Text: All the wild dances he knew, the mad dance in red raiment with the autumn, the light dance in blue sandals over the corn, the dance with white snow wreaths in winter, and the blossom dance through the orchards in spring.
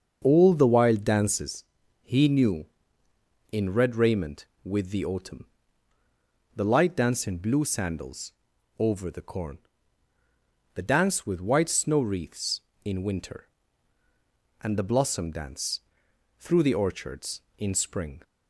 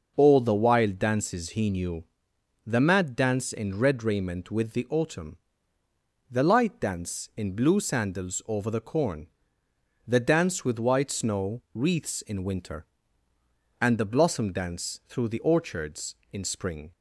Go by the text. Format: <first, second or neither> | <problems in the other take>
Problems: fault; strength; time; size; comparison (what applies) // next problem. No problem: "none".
second | starts louder than the rest; until 1.2 s; 6.5 dB // pauses between "dances" and "he"; slight; at 1.6 s; 0.36 s long // skips "the mad dance"; at 3.0 s // pauses between "sandals" and "over"; noticeable; at 8.3 s; 0.48 s long // pauses between "dance" and "through"; noticeable; at 15.8 s; 0.58 s long